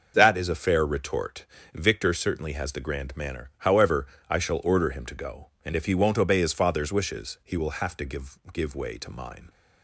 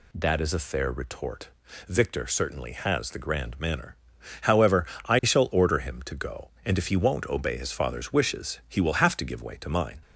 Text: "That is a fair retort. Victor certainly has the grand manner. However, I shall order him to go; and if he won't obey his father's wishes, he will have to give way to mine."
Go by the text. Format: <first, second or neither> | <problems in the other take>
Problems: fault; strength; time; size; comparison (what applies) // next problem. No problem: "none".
second | starts louder than the rest; noticeable; until 1.1 s; 6 dB // says "give" twice; at 8.5 s